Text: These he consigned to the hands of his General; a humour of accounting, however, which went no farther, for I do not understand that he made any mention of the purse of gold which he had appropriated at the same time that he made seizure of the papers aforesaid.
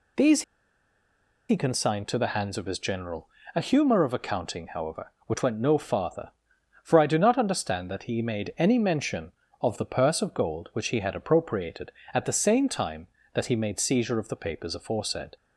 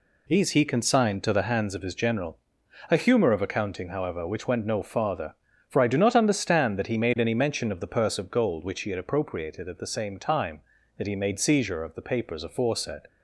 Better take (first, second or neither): second